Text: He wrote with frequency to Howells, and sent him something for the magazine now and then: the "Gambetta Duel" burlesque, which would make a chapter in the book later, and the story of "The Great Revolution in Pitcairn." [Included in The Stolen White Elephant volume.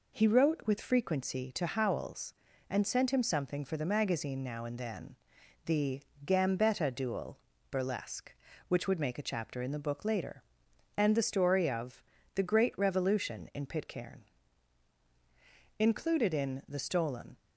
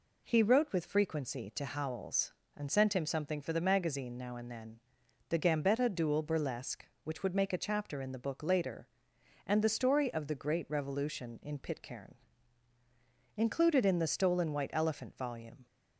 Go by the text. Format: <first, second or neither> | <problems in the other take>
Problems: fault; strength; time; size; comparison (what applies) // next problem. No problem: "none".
second | pauses between "the" and "Gambetta"; slight; at 6.0 s; 0.20 s long // pauses between "Duel" and "burlesque"; slight; at 7.4 s; 0.32 s long // pauses between "of" and "The"; slight; at 12.0 s; 0.36 s long // stops before "White Elephant volume"; at 17.3 s